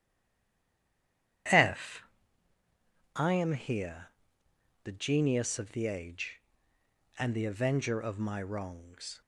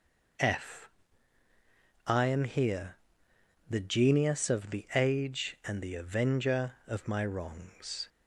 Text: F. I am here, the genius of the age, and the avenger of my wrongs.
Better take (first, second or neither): second